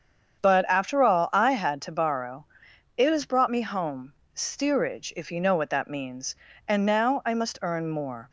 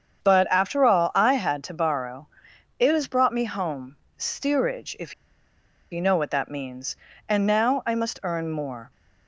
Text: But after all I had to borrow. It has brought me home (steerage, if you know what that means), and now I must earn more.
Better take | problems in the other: first | starts louder than the rest; strong; until 1.3 s; 7.5 dB; strong in the first // pauses between "if" and "you"; noticeable; at 5.1 s; 0.78 s long

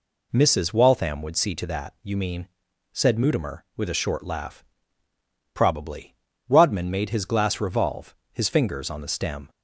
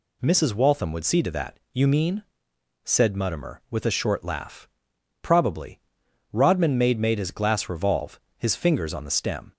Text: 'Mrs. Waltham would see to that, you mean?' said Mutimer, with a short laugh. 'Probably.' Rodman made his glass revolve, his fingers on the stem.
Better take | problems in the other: first | says "made" twice; at 6.9 s

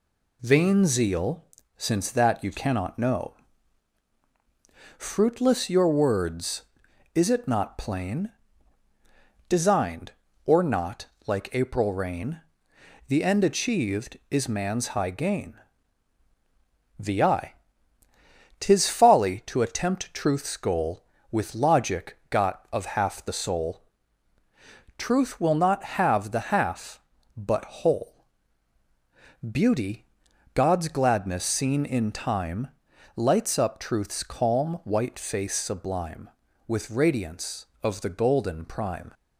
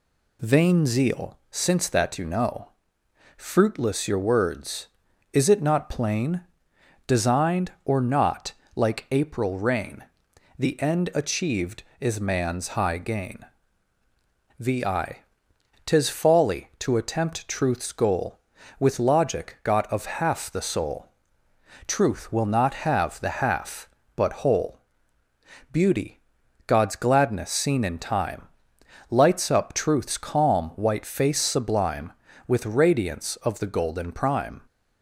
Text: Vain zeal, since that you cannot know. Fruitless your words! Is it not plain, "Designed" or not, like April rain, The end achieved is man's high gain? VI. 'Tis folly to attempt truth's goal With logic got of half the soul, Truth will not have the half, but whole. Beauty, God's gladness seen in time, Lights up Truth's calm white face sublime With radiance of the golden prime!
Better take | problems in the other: first | skips "cannot"; at 2.2 s

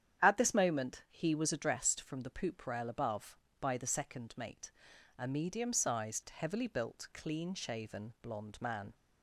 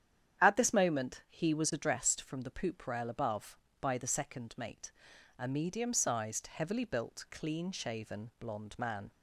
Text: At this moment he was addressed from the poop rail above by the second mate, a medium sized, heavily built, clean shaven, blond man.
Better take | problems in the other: neither | starts louder than the rest; strong; the same in both

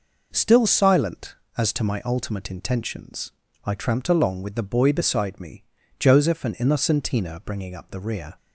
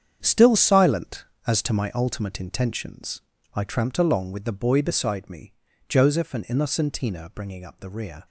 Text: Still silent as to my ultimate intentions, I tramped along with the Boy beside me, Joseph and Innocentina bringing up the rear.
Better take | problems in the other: first | gets quieter; strong; throughout; 11.5 dB

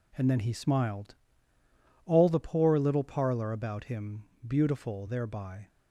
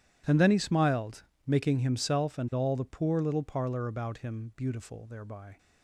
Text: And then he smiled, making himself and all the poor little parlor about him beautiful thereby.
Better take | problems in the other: second | skips "making himself and"; at 1.5 s // pauses between "him" and "beautiful"; slight; at 4.2 s; 0.22 s long

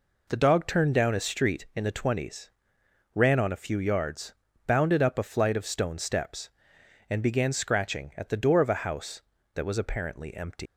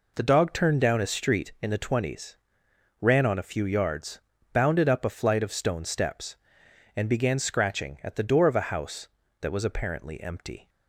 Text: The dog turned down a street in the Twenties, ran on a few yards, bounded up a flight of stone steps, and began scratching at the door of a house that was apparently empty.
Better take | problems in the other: second | leaves "empty" unfinished; at 10.6 s; 170 ms

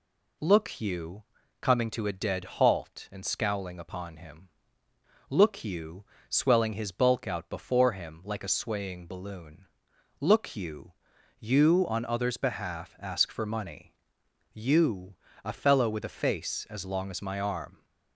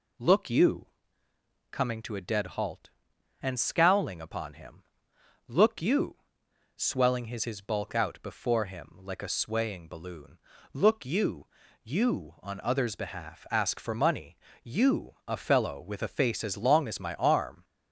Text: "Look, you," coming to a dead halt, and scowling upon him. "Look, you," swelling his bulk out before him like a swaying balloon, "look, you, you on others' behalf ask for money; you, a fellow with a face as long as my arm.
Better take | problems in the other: first | says "his" twice; at 7.4 s

